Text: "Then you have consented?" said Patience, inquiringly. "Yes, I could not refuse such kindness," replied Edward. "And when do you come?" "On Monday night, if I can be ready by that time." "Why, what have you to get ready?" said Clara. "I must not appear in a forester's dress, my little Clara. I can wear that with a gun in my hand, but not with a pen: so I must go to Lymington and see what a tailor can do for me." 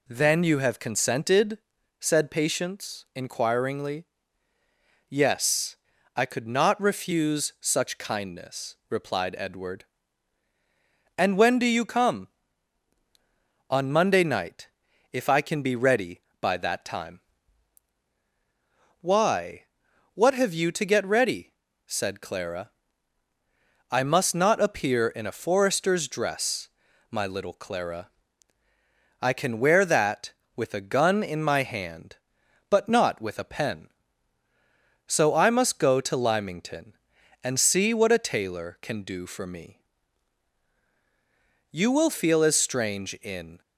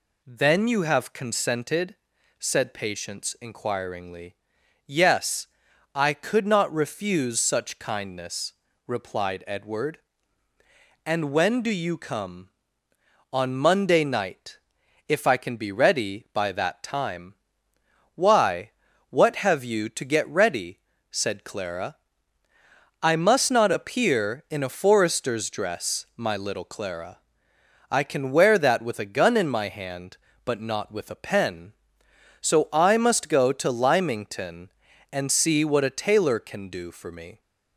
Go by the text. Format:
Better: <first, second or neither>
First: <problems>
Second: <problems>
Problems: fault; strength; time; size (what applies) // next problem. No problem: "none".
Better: second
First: goes on to say "You will feel as strange in"; strong; from 41.7 s on; 1.9 s long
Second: none